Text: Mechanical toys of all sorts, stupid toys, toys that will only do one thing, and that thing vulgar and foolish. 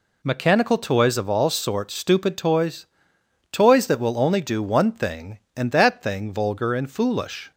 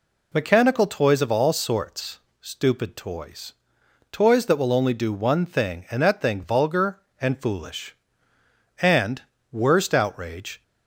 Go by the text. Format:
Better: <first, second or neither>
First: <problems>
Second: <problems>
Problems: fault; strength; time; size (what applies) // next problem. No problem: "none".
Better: first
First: none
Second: goes on to say "And worst outrage"; strong; from 8.8 s on; 1.8 s long